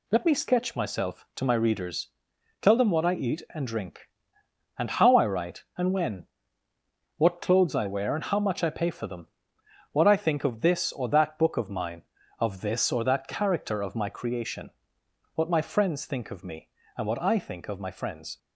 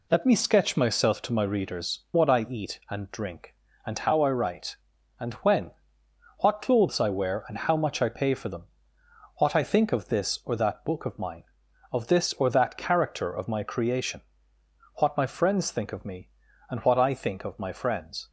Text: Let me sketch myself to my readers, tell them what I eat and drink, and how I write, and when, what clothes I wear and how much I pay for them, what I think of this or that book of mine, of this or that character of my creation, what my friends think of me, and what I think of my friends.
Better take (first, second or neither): first